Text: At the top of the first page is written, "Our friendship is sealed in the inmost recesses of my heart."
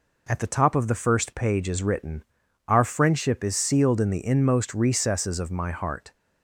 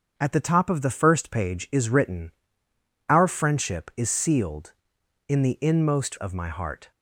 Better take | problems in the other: first | starts louder than the rest; until 1.1 s; 7 dB // skips "recesses"; at 6.1 s

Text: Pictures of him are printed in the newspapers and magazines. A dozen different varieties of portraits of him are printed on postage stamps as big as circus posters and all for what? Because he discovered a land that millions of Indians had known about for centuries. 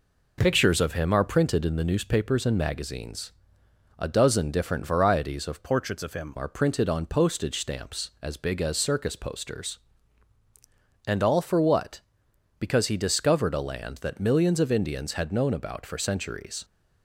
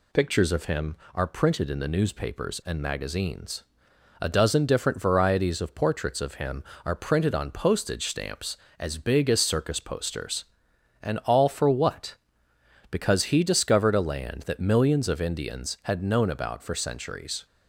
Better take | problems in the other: second | changes voice from "portraits" to "him"; from 5.6 to 6.3 s; 0.7 s long

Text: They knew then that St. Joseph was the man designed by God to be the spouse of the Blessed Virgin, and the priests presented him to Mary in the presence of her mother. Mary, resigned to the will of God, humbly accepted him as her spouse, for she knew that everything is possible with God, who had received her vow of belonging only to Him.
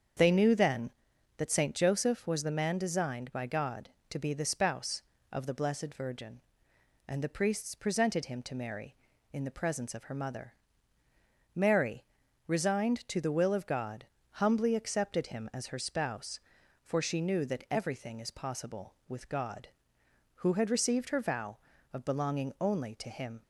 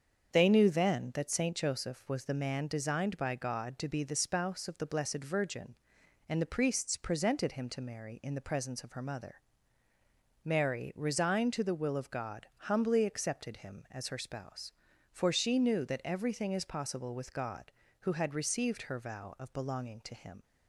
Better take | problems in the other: first | starts louder than the rest; strong; until 1.3 s; 7 dB; strong in the first // skips "only"; at 20.0 s

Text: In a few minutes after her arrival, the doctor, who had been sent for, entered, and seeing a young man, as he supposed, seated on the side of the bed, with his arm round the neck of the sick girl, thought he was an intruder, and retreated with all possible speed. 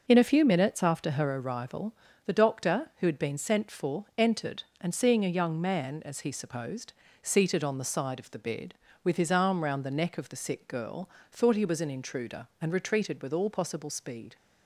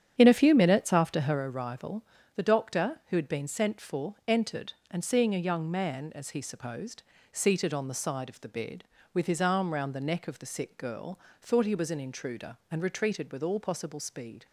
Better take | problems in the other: first | starts louder than the rest; strong; until 1.4 s; 9 dB

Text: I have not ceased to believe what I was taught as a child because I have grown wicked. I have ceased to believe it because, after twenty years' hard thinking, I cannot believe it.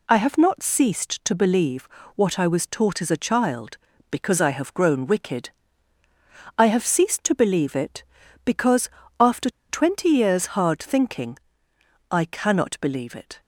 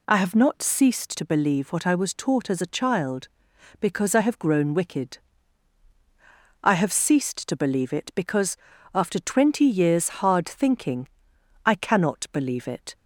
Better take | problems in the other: second | pauses between "believe" and "what"; slight; at 1.8 s; 0.30 s long // pauses between "after" and "twenty"; slight; at 9.4 s; 0.20 s long

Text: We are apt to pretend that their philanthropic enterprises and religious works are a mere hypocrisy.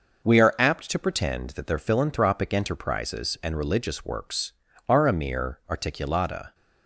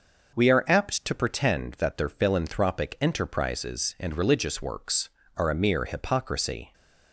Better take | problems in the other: second | says "articulata" for "hypocrisy"; at 5.6 s

